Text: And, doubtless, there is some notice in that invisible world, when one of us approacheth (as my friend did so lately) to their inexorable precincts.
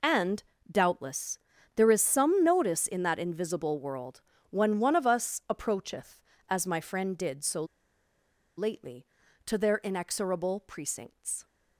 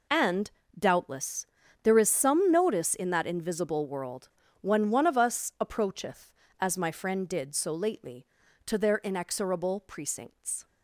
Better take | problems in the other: second | pauses between "so" and "lately"; noticeable; at 7.6 s; 0.93 s long

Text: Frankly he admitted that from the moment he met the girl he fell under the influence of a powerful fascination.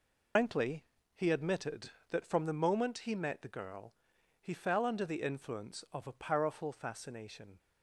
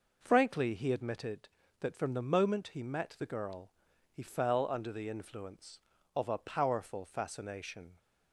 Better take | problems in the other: second | loses the start of "Frankly"; at 0.3 s; 130 ms // pauses between "Frankly" and "he"; slight; at 0.8 s; 0.32 s long // pauses between "girl" and "he"; noticeable; at 3.9 s; 0.48 s long; also in the second

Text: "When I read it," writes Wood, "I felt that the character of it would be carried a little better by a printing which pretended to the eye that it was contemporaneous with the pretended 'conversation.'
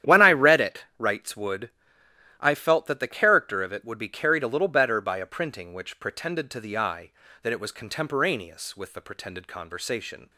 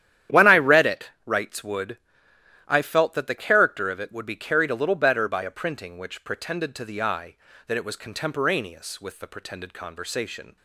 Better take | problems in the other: neither | starts louder than the rest; strong; the same in both

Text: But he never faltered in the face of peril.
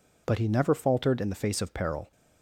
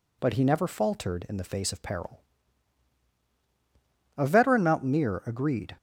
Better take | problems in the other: first | goes on to say "A veteran mountaineer agreed"; from 4.1 s on; 1.6 s long

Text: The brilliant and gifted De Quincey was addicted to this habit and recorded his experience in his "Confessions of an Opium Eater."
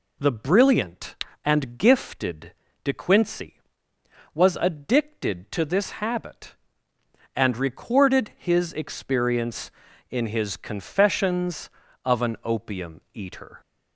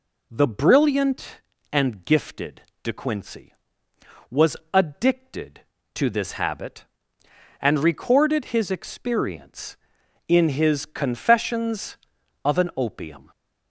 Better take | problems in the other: first | pauses between "gifted" and "De"; slight; at 2.6 s; 0.20 s long; slight in the first // pauses between "was" and "addicted"; slight; at 4.5 s; 0.16 s long // stops before "Eater"; at 13.3 s

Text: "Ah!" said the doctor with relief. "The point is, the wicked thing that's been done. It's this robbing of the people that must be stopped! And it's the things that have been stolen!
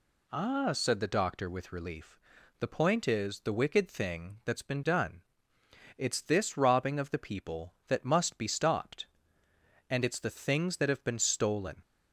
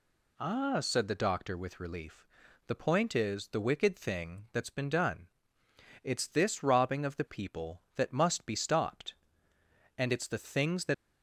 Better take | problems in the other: first | stops before "have been stolen"; at 10.9 s

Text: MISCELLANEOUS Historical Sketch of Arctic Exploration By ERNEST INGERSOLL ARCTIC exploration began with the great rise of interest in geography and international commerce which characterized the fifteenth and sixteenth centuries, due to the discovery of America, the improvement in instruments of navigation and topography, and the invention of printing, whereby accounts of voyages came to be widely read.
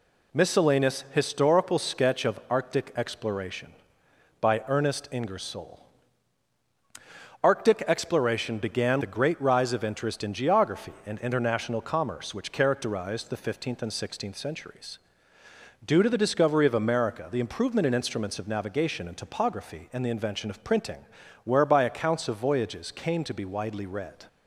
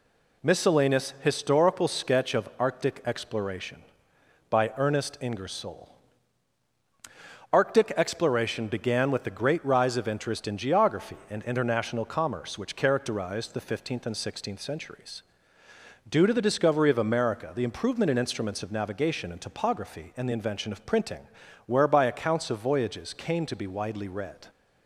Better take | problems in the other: second | pauses between "INGERSOLL" and "ARCTIC"; strong; at 5.7 s; 1.6 s long; strong in the second // skips "with"; at 9.0 s

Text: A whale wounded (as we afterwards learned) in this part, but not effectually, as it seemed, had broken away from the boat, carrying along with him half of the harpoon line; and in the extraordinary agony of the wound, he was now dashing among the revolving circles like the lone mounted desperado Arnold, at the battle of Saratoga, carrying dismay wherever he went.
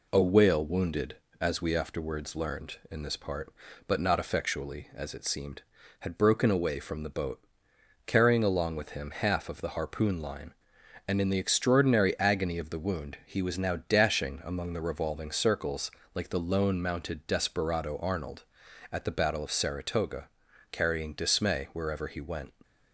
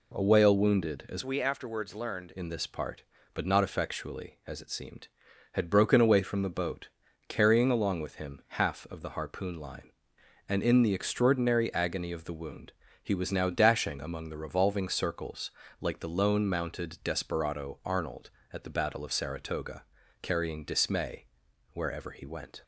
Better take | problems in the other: first | changes voice from "we" to "learned"; from 1.2 to 2.3 s; 1.1 s long // pauses between "circles" and "like"; slight; at 15.5 s; 0.28 s long; slight in the first // pauses between "dismay" and "wherever"; noticeable; at 21.2 s; 0.46 s long

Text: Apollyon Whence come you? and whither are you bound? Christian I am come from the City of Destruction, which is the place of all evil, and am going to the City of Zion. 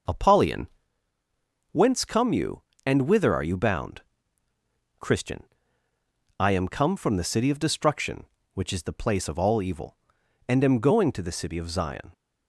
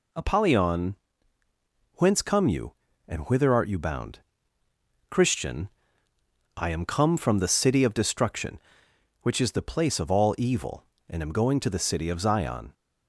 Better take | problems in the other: first | pauses between "Apollyon" and "Whence"; noticeable; at 0.9 s; 0.96 s long; also in the first // says "art" for "are"; at 3.5 s // pauses between "Christian" and "I"; noticeable; at 5.6 s; 0.88 s long; noticeable in the first

